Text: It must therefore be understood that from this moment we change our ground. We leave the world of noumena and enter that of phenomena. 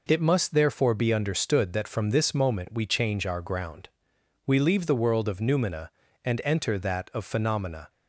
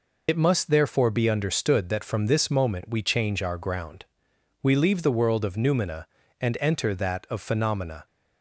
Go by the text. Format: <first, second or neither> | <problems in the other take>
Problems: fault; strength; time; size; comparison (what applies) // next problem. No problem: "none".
first | loses the start of "It"; at 0.2 s; 60 ms